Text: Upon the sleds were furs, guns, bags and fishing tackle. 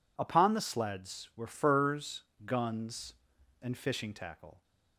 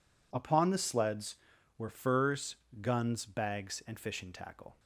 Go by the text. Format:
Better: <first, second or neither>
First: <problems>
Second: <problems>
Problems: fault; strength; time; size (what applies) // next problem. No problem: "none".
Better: second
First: skips "bags"; at 3.3 s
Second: none